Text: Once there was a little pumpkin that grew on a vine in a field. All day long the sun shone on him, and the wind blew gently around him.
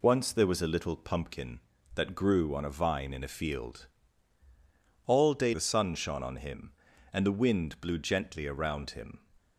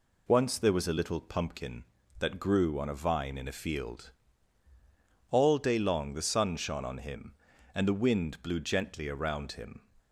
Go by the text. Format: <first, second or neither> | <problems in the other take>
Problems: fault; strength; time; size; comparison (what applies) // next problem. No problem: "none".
second | skips "long"; at 5.5 s